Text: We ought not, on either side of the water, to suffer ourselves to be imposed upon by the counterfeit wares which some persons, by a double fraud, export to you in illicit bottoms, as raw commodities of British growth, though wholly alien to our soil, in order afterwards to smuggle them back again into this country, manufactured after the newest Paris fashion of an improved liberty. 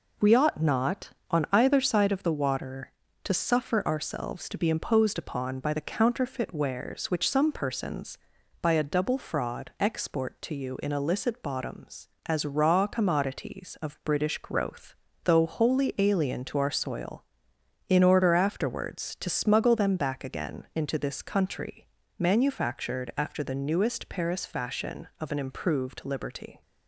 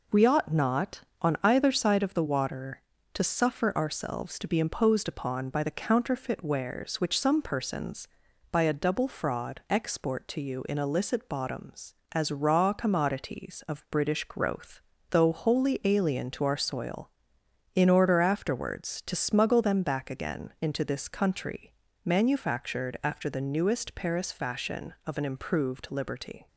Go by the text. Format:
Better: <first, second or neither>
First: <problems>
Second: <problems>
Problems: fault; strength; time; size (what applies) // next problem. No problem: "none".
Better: neither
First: none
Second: none